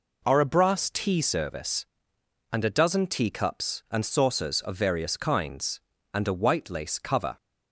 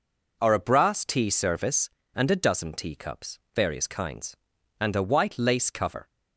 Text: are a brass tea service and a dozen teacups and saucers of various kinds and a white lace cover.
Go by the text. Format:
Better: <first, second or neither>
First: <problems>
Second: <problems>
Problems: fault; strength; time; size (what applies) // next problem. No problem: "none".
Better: first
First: none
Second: skips "and saucers of"; at 3.4 s